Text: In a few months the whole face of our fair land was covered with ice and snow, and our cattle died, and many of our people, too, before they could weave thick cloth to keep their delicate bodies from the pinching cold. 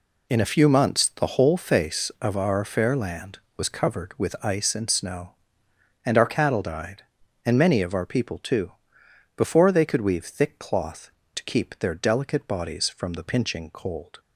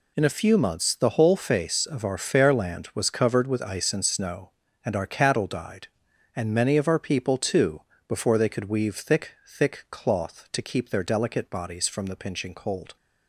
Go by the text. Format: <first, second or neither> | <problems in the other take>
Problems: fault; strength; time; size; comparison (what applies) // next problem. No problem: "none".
first | says "thick" twice; at 9.4 s